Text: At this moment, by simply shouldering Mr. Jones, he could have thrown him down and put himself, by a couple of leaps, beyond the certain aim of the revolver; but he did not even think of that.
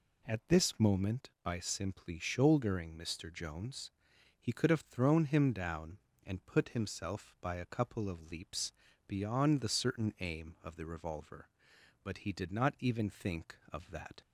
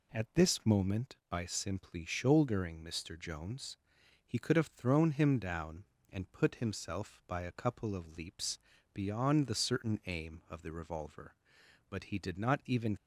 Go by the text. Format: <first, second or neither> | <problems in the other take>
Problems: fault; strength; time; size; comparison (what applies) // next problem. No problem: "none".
first | stops before "think of that"; at 12.9 s